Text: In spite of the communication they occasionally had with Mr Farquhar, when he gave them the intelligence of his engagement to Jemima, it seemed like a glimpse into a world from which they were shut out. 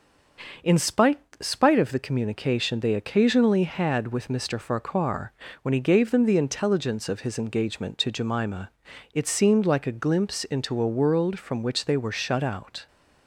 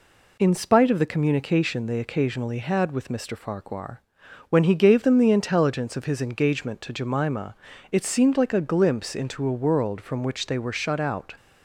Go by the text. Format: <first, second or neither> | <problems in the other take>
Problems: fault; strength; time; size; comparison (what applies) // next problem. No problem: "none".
second | says "spite" twice; at 1.4 s